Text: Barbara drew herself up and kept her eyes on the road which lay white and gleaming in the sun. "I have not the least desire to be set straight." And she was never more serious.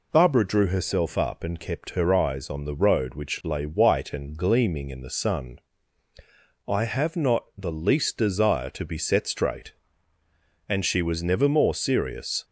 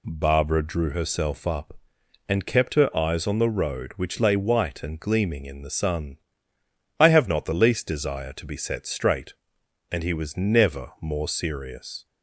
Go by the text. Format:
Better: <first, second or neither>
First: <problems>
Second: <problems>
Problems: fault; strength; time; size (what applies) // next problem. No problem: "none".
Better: first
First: none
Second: says "he" for "she"; at 10.0 s